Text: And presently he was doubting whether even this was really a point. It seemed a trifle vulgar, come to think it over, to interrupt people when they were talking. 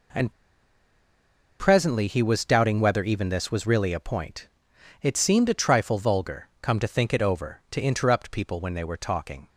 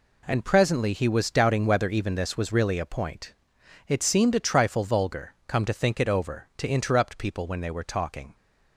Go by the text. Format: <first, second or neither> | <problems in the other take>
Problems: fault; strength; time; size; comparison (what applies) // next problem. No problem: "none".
second | pauses between "And" and "presently"; strong; at 0.3 s; 1.2 s long